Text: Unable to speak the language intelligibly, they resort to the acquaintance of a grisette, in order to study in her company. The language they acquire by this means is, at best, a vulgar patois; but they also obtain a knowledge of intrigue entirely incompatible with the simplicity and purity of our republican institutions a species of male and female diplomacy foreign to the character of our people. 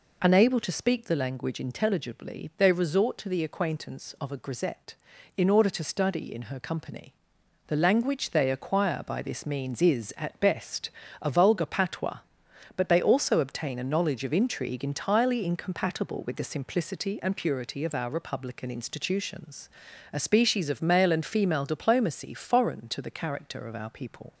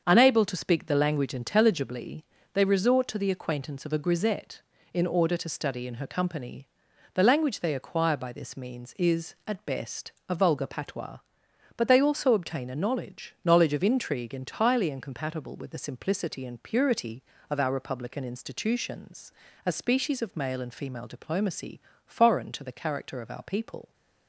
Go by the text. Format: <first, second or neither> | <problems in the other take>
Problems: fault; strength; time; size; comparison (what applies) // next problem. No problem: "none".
first | starts louder than the rest; until 1.0 s; 7 dB // says "knowledge" twice; at 13.4 s // pauses between "institutions" and "a"; slight; at 19.3 s; 0.34 s long; also in the first // pauses between "diplomacy" and "foreign"; slight; at 21.7 s; 0.26 s long